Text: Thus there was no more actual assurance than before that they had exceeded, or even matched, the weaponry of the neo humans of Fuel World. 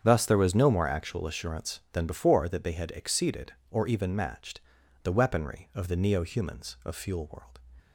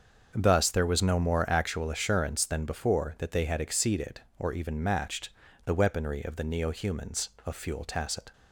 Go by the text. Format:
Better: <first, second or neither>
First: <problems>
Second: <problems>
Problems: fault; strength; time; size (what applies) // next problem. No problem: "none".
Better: first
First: starts louder than the rest; strong; until 1.0 s; 8 dB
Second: starts louder than the rest; until 1.3 s; 6.5 dB // says "Tacit" for "World"; at 7.8 s